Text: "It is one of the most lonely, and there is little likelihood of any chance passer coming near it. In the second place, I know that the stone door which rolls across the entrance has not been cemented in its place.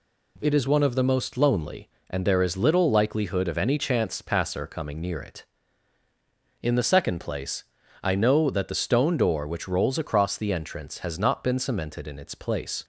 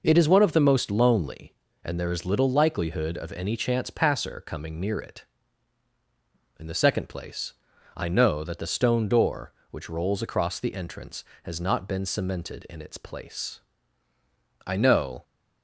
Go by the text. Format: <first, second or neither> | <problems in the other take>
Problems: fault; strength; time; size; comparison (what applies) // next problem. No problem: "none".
first | goes on to say "I know"; from 14.6 s on; 0.56 s long